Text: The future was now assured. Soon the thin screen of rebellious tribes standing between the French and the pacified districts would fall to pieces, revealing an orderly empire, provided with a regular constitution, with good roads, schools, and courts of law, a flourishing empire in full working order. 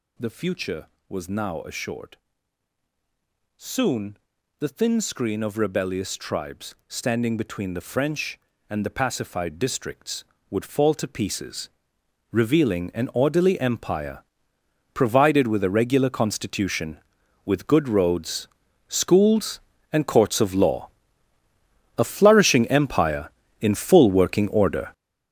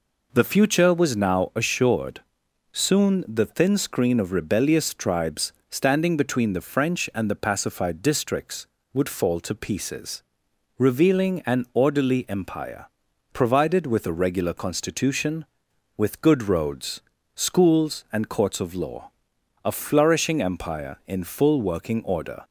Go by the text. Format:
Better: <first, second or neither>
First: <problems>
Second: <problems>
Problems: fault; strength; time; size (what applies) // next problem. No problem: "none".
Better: second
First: gets louder; strong; throughout; 11 dB // pauses between "Soon" and "the"; at 4.1 s; 0.42 s long // pauses between "tribes" and "standing"; slight; at 6.7 s; 0.16 s long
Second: pauses between "tribes" and "standing"; slight; at 5.5 s; 0.20 s long